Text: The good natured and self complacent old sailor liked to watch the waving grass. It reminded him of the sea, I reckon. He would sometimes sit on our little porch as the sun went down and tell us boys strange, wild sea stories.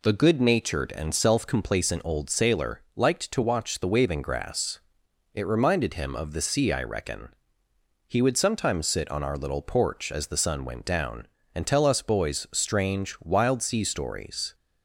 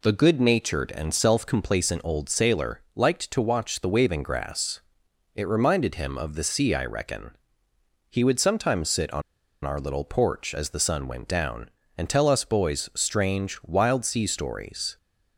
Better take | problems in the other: first | pauses between "on" and "our"; at 9.2 s; 0.43 s long

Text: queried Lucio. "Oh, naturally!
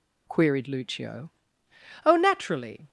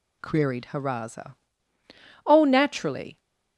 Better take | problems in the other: first | says "Haraza" for "Lucio"; at 0.7 s

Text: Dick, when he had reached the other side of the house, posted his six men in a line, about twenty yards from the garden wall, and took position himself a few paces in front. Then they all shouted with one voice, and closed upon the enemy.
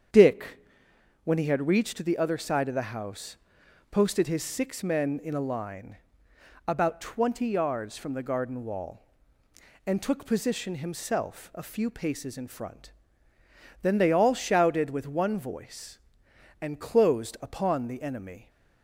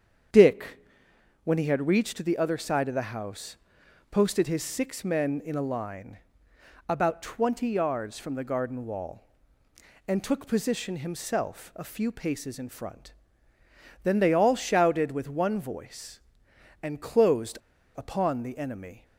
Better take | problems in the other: first | starts louder than the rest; strong; until 1.9 s; 8 dB; strong in the first // pauses between "closed" and "upon"; slight; at 17.5 s; 0.36 s long

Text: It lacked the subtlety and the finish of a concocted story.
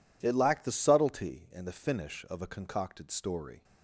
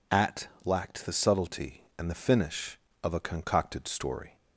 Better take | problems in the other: first | says "At" for "It"; at 0.1 s

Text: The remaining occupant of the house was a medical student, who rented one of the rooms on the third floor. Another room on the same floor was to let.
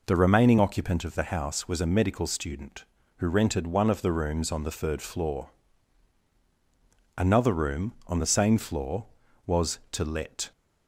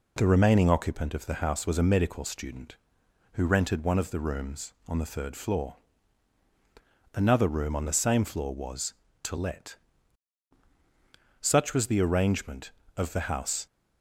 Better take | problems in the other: first | goes on to say "Such was the arrangement of the house"; strong; from 11.3 s on; 2.2 s long

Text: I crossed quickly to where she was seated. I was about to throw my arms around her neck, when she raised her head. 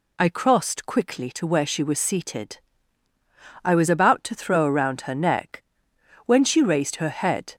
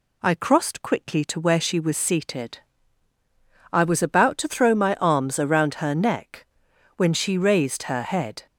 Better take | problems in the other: second | skips "my arms"; at 4.6 s

